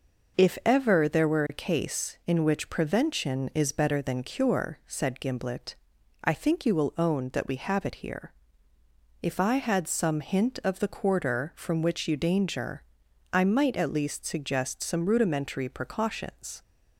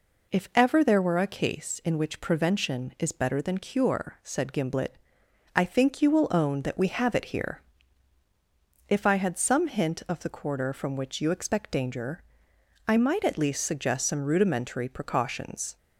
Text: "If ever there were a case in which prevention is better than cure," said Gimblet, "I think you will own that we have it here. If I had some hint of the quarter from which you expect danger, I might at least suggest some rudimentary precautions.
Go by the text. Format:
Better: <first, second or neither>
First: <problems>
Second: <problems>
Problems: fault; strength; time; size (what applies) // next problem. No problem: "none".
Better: second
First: skips "expect"; at 12.1 s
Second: none